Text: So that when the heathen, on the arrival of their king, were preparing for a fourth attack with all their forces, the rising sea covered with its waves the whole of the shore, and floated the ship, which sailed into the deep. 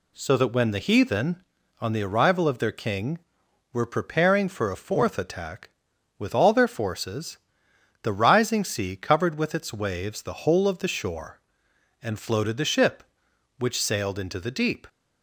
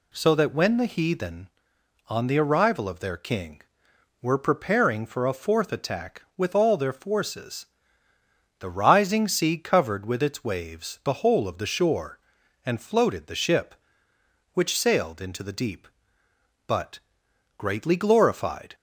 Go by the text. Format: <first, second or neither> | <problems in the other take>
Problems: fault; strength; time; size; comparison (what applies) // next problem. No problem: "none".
first | goes on to say "But greatly glorified"; strong; from 16.6 s on; 2.0 s long